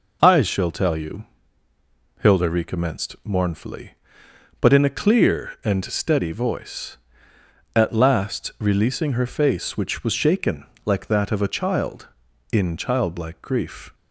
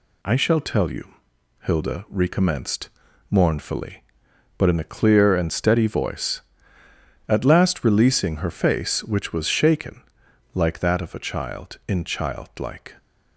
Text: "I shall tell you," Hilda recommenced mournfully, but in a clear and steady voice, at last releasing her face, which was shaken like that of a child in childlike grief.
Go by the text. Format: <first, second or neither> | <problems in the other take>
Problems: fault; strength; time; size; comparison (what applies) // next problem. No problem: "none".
first | pauses between "recommenced" and "mournfully"; at 2.8 s; 0.40 s long // pauses between "shaken" and "like"; noticeable; at 10.0 s; 0.52 s long; slight in the first // stops before "grief"; at 12.9 s